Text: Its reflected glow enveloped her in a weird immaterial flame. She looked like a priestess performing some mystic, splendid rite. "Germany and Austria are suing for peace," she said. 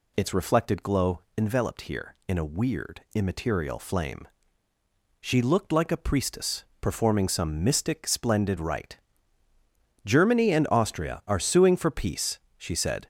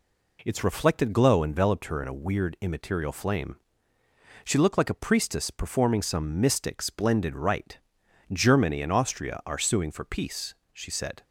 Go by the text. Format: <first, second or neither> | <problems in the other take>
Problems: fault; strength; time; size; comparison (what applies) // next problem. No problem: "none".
second | pauses between "glow" and "enveloped"; slight; at 1.1 s; 0.16 s long // says "here" for "her"; at 1.8 s // pauses between "priestess" and "performing"; slight; at 6.6 s; 0.18 s long